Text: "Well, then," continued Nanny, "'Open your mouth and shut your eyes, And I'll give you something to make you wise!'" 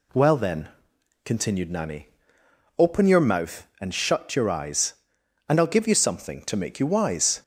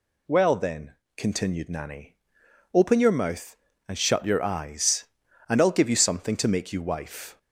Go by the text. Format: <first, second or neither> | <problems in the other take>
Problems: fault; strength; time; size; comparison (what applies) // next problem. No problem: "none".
first | says "wife" for "wise"; at 6.8 s